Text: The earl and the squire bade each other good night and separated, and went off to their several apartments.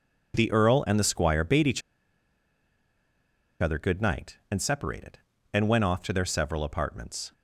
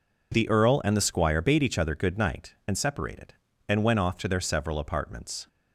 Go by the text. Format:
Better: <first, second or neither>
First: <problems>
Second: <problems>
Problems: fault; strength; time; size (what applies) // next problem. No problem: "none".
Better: second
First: pauses between "each" and "other"; strong; at 1.8 s; 1.7 s long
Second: none